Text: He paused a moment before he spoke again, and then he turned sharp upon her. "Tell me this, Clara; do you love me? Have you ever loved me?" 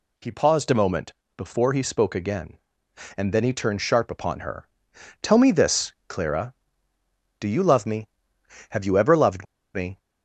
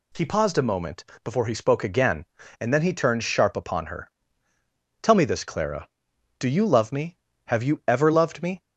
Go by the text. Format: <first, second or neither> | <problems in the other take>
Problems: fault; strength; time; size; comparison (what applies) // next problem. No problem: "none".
second | pauses between "moment" and "before"; slight; at 1.1 s; 0.24 s long; slight in the second // pauses between "loved" and "me"; slight; at 9.4 s; 0.29 s long